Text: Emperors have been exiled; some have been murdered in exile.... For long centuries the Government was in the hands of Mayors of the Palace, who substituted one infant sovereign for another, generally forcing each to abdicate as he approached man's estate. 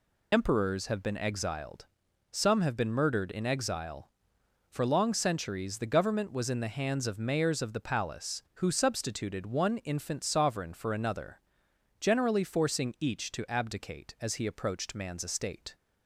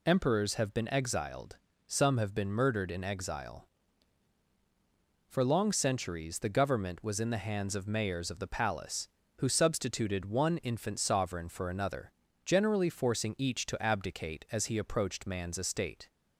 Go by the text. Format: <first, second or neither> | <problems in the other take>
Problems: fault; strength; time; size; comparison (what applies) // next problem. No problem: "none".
second | loses the start of "Emperors"; at 0.3 s; 45 ms